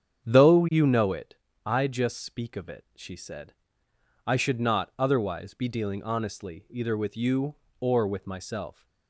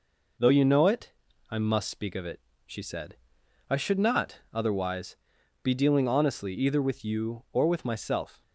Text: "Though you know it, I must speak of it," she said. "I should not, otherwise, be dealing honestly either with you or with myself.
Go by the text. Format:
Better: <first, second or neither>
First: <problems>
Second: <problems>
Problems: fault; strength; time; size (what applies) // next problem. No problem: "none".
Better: second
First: starts louder than the rest; strong; until 1.2 s; 8.5 dB // says "just" for "must"; at 1.8 s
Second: none